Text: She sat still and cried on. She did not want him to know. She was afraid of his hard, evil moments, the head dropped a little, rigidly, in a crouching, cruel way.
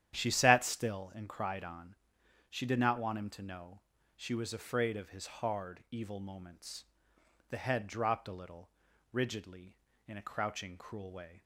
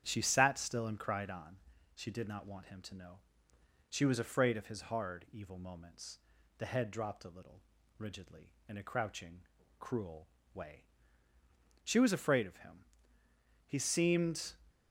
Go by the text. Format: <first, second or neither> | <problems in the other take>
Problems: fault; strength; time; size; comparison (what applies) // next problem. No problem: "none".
first | starts louder than the rest; strong; until 1.0 s; 9.5 dB; strong in the first // pauses between "cruel" and "way"; slight; at 10.2 s; 0.26 s long // goes on to say "She was afraid of him He seemed"; strong; from 11.8 s on; 2.7 s long